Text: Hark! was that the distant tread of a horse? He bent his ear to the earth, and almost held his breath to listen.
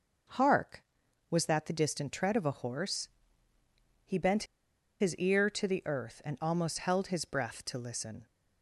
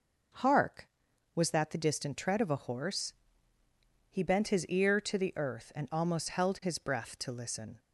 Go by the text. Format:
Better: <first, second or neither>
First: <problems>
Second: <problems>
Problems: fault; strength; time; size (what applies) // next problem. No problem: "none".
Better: second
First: pauses between "bent" and "his"; noticeable; at 4.4 s; 0.57 s long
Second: none